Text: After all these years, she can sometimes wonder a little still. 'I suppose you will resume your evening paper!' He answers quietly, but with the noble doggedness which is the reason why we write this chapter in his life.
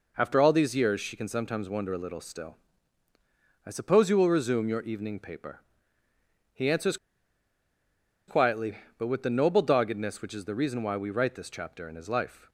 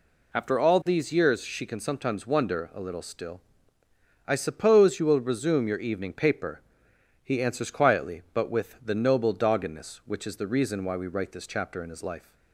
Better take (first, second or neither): second